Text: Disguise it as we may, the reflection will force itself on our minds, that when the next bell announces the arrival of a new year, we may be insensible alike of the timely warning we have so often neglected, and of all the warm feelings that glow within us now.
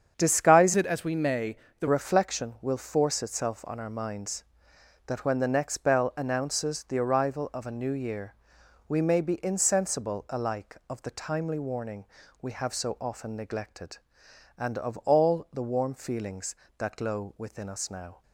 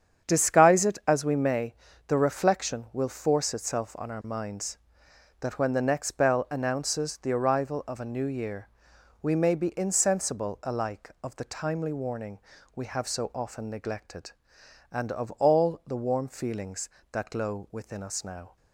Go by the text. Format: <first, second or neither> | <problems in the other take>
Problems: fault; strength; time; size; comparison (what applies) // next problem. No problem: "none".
second | starts louder than the rest; strong; until 1.1 s; 7.5 dB; strong in the second // changes voice from "it" to "the"; from 0.7 to 1.8 s; 1.1 s long // pauses between "warning" and "we"; slight; at 12.0 s; 0.34 s long; slight in the second